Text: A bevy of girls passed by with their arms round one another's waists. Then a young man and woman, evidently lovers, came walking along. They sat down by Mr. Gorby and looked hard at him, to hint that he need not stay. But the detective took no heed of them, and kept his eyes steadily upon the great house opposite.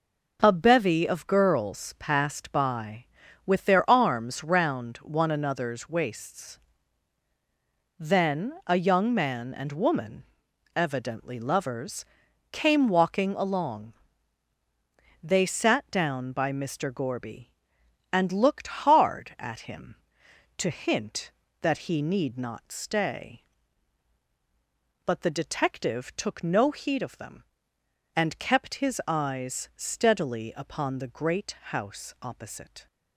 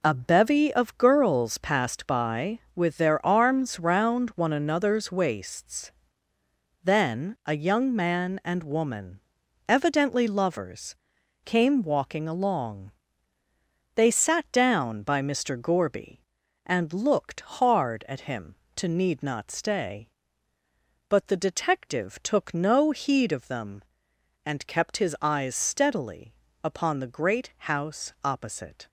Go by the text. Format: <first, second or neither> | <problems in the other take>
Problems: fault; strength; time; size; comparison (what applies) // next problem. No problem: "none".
first | skips "hint that he"; at 18.8 s // pauses between "steadily" and "upon"; slight; at 26.3 s; 0.30 s long // pauses between "great" and "house"; slight; at 27.5 s; 0.18 s long